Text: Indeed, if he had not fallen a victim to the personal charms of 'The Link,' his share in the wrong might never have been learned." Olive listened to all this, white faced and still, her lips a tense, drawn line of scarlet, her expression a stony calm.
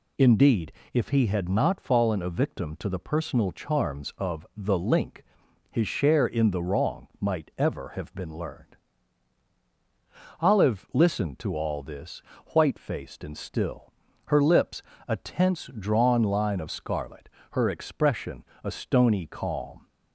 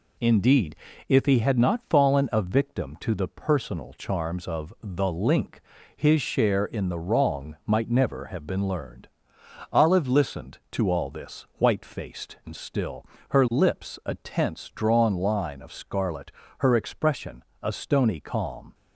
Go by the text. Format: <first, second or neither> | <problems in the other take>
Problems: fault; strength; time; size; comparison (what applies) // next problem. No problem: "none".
second | says "ever" for "never"; at 7.5 s // pauses between "lips" and "a"; slight; at 14.8 s; 0.24 s long // pauses between "expression" and "a"; slight; at 18.4 s; 0.18 s long; slight in the second